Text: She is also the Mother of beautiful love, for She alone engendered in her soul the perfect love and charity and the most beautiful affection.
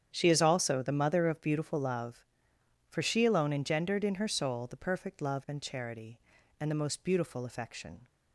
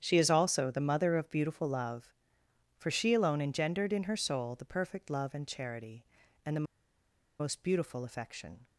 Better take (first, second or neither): first